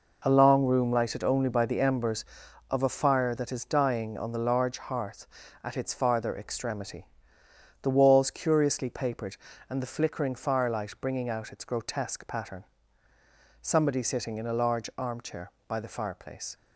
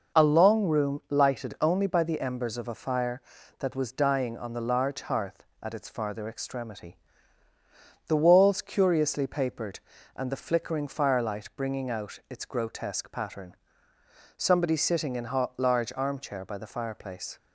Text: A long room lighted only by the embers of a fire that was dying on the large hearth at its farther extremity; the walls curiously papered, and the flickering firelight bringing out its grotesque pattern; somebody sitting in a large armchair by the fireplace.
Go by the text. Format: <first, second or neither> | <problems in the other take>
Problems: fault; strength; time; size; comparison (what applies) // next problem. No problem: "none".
second | says "is" for "was"; at 3.5 s